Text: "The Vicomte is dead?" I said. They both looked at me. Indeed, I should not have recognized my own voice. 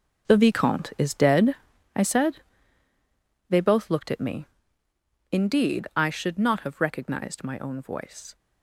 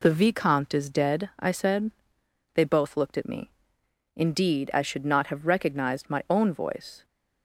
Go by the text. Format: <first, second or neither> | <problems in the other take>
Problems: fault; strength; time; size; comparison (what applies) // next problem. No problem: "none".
second | gets quieter; strong; throughout; 12 dB